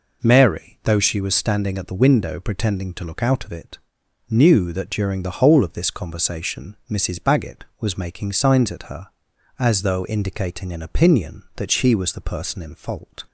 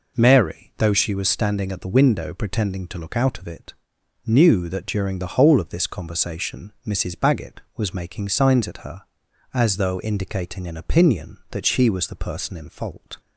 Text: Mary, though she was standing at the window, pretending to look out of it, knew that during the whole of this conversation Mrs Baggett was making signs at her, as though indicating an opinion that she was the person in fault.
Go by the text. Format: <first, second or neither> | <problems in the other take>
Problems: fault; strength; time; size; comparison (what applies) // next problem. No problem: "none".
neither | none